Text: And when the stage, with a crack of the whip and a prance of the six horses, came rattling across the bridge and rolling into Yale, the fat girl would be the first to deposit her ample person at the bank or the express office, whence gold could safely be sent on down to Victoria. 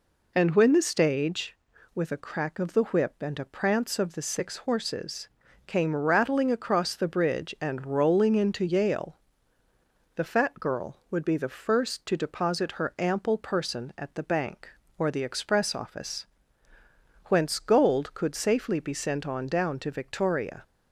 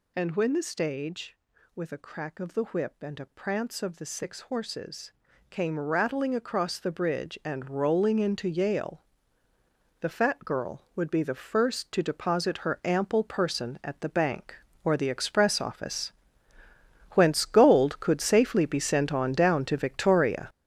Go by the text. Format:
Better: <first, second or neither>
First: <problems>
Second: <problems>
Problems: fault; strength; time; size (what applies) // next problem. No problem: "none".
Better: first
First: none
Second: gets louder; strong; throughout; 8.5 dB